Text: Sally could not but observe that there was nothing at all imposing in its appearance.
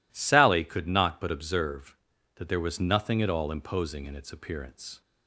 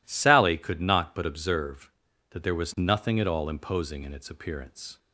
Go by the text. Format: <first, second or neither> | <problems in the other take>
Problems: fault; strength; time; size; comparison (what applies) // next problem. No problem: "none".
neither | none